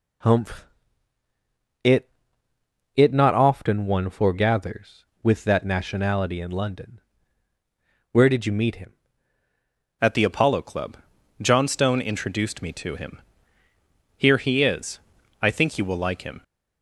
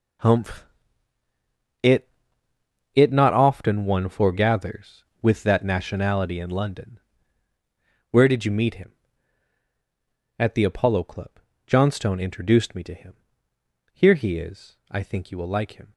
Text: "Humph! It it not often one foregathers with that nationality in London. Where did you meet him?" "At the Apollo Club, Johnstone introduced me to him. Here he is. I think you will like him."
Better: second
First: pauses between "It" and "it"; noticeable; at 2.1 s; 0.86 s long // changes voice at "At"; from 9.9 s on; 6.5 s long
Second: pauses between "It" and "it"; noticeable; at 2.0 s; 0.86 s long

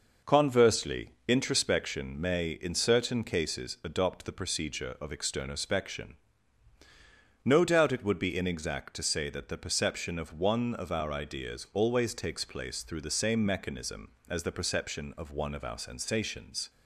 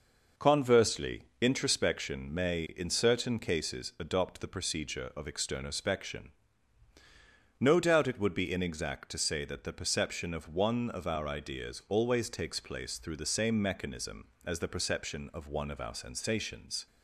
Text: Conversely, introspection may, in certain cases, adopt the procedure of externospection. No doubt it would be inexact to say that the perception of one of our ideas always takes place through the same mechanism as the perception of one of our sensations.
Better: neither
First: none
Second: none

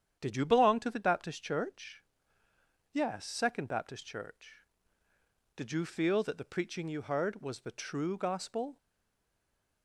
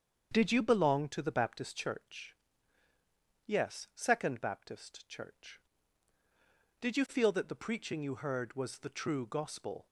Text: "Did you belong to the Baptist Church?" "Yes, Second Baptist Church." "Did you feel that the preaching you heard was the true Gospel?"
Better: second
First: starts louder than the rest; strong; until 1.2 s; 9 dB // stays silent after the last word; from 8.7 s on; 1.1 s long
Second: starts louder than the rest; strong; until 1.3 s; 7.5 dB

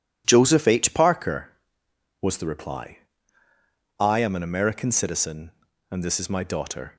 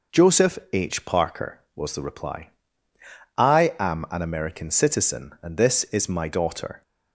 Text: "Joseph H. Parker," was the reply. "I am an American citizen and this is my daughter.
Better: neither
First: none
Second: none

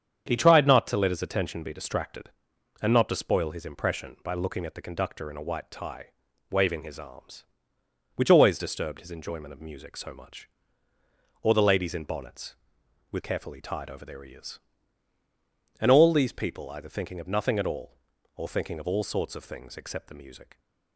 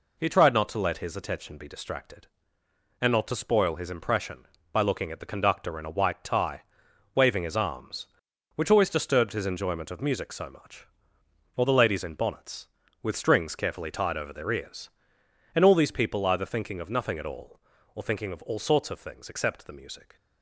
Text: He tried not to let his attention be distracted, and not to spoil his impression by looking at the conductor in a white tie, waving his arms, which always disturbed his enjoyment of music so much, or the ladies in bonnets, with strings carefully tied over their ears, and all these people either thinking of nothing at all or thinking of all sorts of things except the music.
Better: second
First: starts louder than the rest; strong; until 1.3 s; 8 dB // skips "strings"; at 13.2 s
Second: none

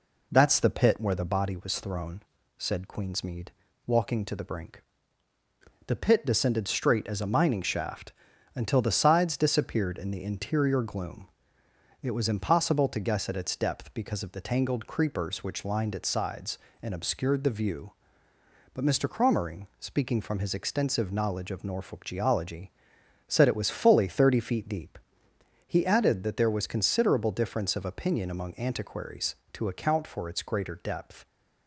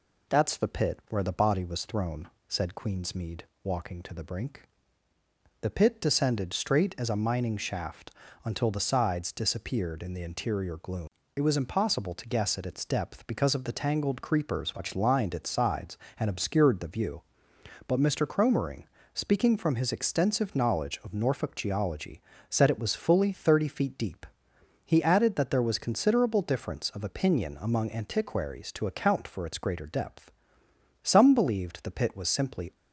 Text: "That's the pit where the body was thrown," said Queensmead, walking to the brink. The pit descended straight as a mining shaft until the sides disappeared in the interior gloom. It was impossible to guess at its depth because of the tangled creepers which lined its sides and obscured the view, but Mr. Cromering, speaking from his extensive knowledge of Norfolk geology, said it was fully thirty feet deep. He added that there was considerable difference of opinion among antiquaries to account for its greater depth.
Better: first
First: pauses between "shaft" and "until"; at 8.1 s; 0.42 s long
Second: pauses between "shaft" and "until"; slight; at 8.1 s; 0.32 s long // goes on to say "Some believed the pit was simply"; strong; from 31.0 s on; 1.7 s long

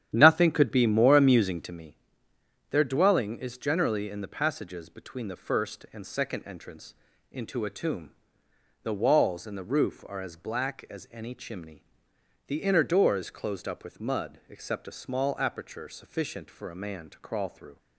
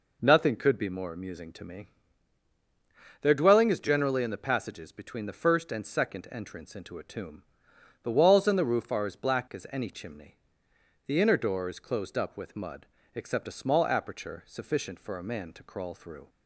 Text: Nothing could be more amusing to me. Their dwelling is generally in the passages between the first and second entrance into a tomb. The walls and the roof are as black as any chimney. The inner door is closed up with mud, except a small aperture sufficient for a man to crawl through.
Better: second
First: starts louder than the rest; strong; until 1.7 s; 10 dB // pauses between "entrance" and "into"; at 6.9 s; 0.38 s long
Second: none

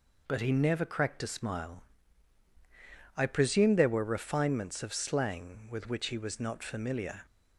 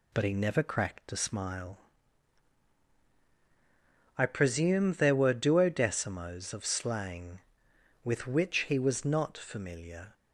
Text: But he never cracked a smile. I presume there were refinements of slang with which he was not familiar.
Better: first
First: none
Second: says "duodecimos" for "refinements"; at 5.3 s

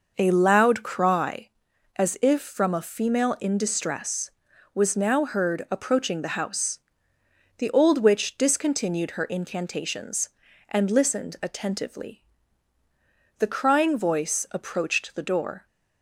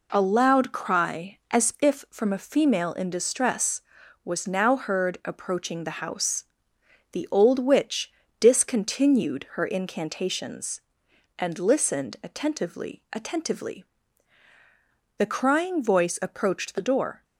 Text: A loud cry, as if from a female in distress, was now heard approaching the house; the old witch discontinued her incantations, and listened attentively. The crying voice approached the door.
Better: first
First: none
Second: pauses between "witch" and "discontinued"; slight; at 8.1 s; 0.30 s long // says "attentively" twice; at 13.1 s

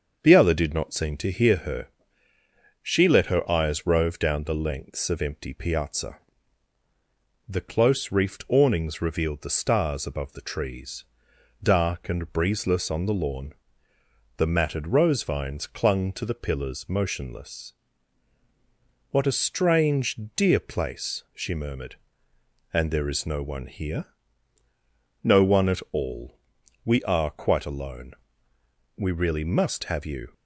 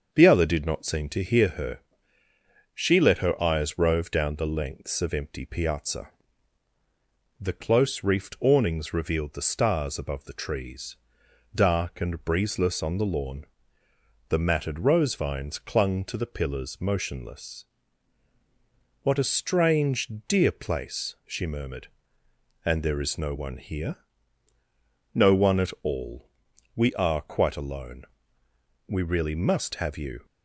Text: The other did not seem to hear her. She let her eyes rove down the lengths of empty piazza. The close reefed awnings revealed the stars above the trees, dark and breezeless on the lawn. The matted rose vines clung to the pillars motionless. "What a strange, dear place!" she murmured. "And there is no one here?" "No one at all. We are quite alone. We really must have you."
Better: neither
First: starts louder than the rest; until 1.2 s; 6.5 dB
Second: starts louder than the rest; until 1.1 s; 6.5 dB

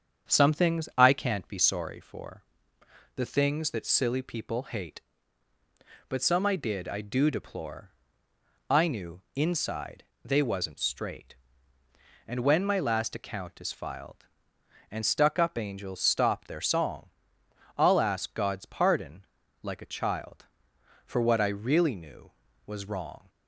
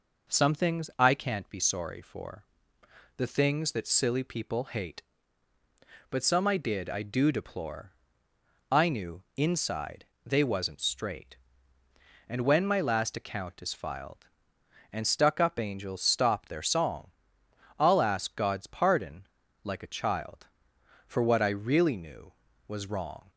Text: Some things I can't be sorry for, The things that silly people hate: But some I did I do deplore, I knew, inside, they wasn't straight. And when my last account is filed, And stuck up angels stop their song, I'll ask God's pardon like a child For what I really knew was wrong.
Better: second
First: starts louder than the rest; strong; until 2.0 s; 8 dB // pauses between "pardon" and "like"; at 19.2 s; 0.38 s long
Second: pauses between "pardon" and "like"; at 19.2 s; 0.38 s long

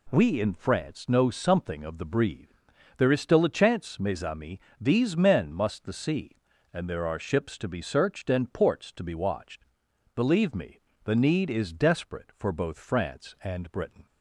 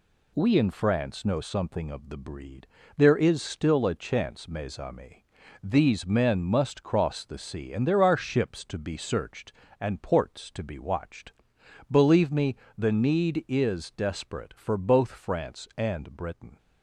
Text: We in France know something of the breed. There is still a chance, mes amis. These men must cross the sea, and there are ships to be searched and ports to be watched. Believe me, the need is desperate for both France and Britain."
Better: second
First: skips "cross"; at 5.8 s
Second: none

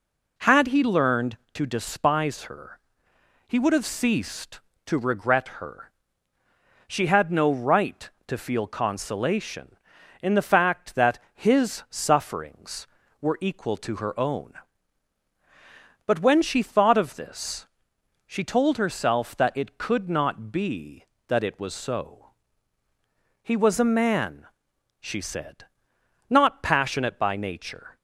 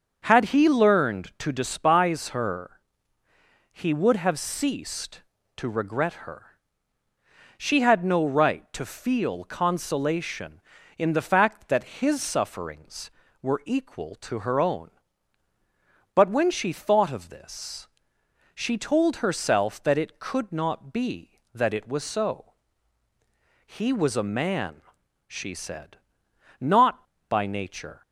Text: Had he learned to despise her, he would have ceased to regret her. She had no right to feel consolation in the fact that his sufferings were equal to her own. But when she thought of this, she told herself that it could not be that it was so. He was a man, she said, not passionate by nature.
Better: first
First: none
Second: starts louder than the rest; until 1.2 s; 6.5 dB // skips "passionate"; at 27.1 s

